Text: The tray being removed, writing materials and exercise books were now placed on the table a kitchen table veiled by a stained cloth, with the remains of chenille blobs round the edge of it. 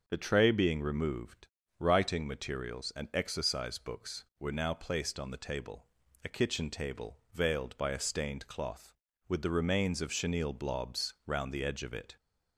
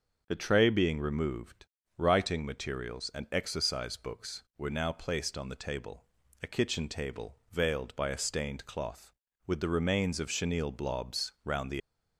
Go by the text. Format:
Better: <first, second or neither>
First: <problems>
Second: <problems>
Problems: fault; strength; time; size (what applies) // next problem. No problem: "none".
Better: first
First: starts louder than the rest; noticeable; until 1.0 s; 6 dB // pauses between "table" and "a"; at 5.8 s; 0.38 s long // pauses between "table" and "veiled"; slight; at 7.1 s; 0.16 s long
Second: starts louder than the rest; until 1.2 s; 6.5 dB // pauses between "table" and "a"; at 6.0 s; 0.38 s long // pauses between "table" and "veiled"; slight; at 7.3 s; 0.16 s long // stops before "edge of it"; at 11.8 s